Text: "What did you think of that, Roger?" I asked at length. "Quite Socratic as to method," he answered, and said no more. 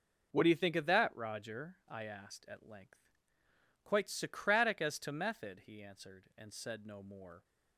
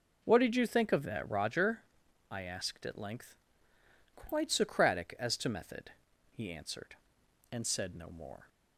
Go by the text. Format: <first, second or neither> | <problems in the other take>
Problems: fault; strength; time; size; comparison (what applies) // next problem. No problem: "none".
second | says "do" for "did"; at 0.4 s